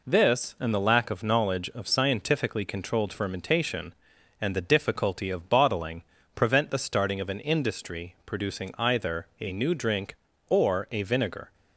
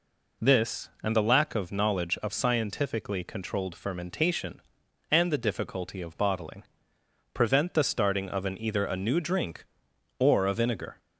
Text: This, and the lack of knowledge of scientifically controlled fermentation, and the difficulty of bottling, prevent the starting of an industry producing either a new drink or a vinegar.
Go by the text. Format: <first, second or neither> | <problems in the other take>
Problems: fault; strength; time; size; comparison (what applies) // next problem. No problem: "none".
first | skips "industry producing"; at 8.5 s